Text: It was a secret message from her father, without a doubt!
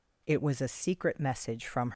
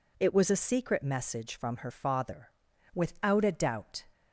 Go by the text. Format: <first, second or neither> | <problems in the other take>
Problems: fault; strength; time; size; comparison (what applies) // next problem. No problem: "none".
second | stops before "her father without a doubt"; at 1.9 s